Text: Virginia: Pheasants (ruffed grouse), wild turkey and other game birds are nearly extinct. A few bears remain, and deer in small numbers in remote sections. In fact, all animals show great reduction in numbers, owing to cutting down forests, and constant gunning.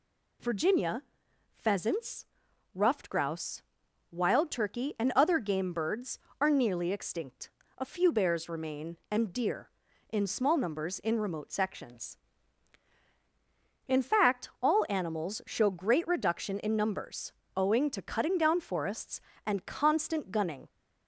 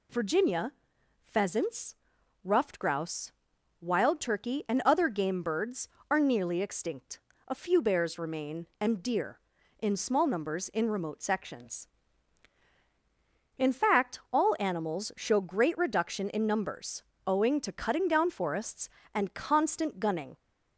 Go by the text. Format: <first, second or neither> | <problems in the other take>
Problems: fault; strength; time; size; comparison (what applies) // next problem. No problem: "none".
neither | none